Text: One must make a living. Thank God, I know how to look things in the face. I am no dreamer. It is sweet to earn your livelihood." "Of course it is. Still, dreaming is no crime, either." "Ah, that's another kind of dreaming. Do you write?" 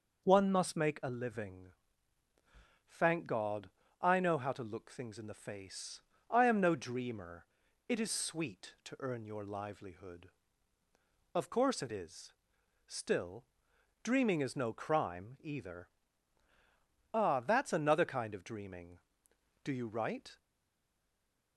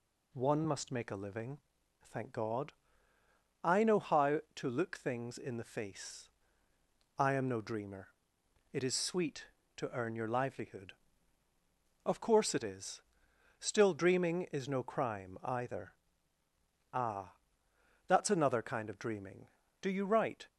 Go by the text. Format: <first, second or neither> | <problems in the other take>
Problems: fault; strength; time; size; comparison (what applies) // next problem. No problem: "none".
second | stays silent after the last word; noticeable; from 20.3 s on; 1.2 s long